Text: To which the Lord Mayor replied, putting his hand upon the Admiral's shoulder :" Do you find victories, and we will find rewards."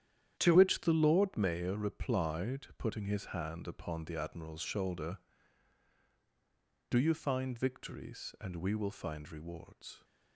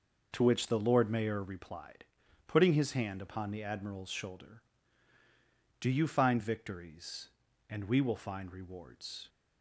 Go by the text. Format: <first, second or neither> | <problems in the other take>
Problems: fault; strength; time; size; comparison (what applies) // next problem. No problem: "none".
second | starts louder than the rest; strong; until 1.4 s; 10.5 dB; also in the second // changes voice at "which"; from 0.5 s on; 9.5 s long